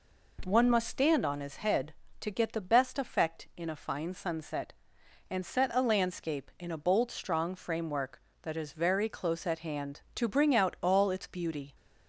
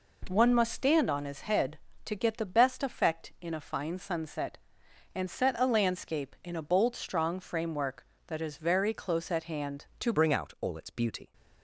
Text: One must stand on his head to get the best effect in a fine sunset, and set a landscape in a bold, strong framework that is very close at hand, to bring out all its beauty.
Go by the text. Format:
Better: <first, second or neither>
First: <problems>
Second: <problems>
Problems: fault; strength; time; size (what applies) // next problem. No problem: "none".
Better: first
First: none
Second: changes voice at "bring"; from 10.1 s on; 1.2 s long